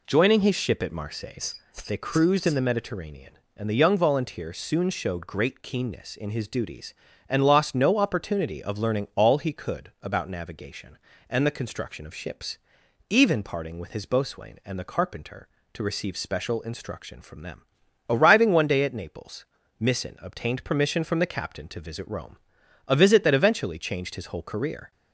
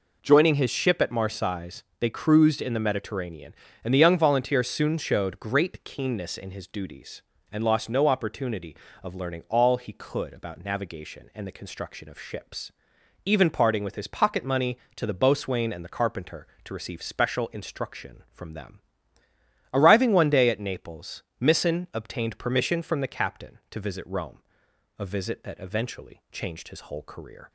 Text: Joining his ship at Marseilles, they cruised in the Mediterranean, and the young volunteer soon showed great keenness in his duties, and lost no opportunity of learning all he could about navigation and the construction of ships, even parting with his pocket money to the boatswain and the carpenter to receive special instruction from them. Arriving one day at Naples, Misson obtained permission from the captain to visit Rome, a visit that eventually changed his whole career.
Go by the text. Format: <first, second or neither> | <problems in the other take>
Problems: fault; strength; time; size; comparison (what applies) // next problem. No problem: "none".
second | skips "pocket money to the"; at 14.0 s